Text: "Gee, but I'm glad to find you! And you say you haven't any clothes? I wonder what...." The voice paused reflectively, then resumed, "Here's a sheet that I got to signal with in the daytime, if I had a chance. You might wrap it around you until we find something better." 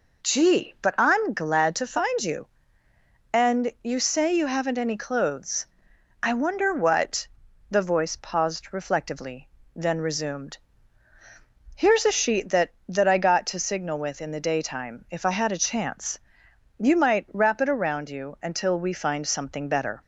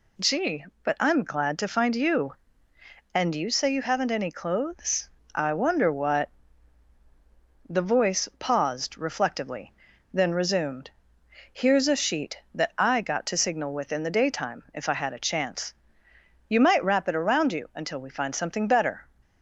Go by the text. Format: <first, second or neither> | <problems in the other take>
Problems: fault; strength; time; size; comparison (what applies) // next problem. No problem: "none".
second | says "that" twice; at 12.8 s